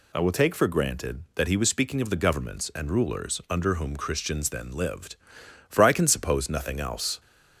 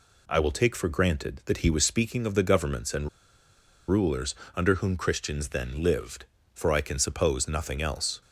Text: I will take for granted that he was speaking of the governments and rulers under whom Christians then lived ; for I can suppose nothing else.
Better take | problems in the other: first | pauses between "and" and "rulers"; noticeable; at 3.0 s; 0.79 s long // pauses between "rulers" and "under"; slight; at 4.3 s; 0.20 s long

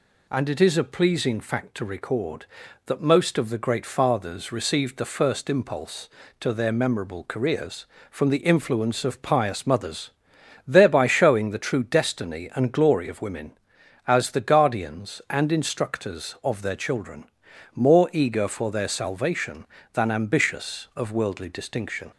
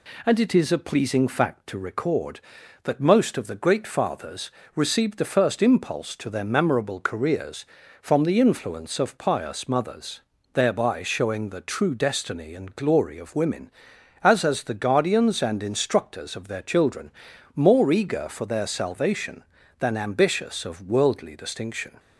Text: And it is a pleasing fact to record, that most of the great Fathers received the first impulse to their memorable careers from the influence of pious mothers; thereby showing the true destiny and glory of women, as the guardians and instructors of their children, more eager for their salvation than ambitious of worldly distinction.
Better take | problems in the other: first | pauses between "Fathers" and "received"; slight; at 4.5 s; 0.24 s long // says "as" twice; at 14.4 s

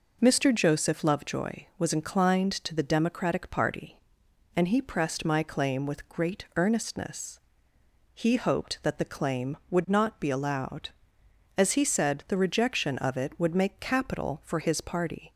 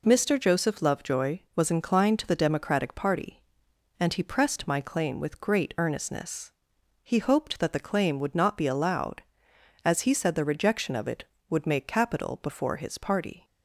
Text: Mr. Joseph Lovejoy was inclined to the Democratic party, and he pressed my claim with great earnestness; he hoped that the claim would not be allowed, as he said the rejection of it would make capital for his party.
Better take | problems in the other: first | says "before" for "for"; at 12.4 s

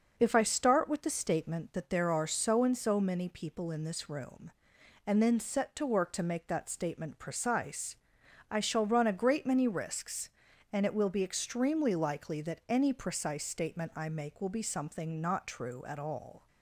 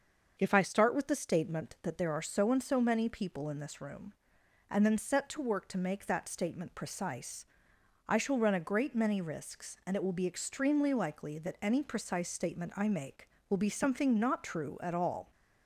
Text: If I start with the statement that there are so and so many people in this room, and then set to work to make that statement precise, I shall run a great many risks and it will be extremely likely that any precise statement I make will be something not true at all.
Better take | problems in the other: neither | starts louder than the rest; the same in both

